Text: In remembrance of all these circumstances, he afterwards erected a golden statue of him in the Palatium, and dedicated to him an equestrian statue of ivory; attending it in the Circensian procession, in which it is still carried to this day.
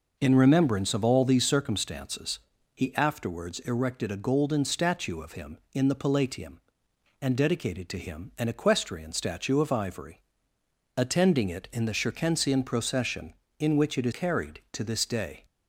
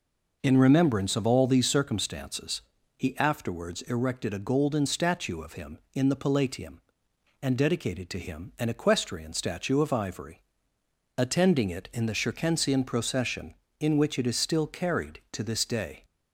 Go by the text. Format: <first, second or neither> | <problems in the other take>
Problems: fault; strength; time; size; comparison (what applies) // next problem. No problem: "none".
second | skips "still"; at 14.1 s